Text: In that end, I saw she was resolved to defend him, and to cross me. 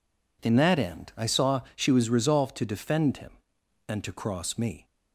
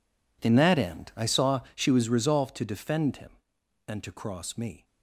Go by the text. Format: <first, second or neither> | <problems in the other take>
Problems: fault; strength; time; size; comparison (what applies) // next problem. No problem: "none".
first | gets quieter; strong; throughout; 19 dB